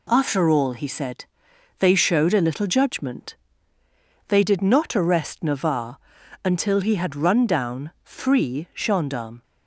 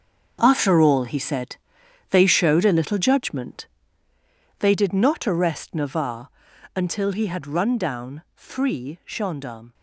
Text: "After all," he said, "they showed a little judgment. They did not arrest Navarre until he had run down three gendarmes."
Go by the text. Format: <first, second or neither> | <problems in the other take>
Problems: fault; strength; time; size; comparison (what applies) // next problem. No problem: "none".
first | gets quieter; strong; throughout; 12 dB // pauses between "Navarre" and "until"; noticeable; at 6.2 s; 0.46 s long; noticeable in the first // pauses between "down" and "three"; slight; at 8.2 s; 0.16 s long; slight in the first